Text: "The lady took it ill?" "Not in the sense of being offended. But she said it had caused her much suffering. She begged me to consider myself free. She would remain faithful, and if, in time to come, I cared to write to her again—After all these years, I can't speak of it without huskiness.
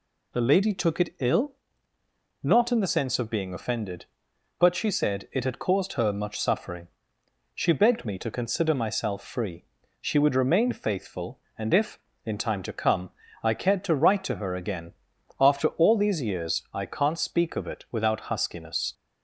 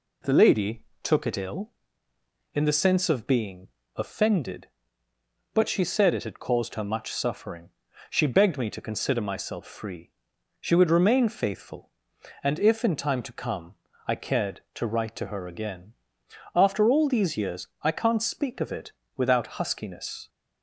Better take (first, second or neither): first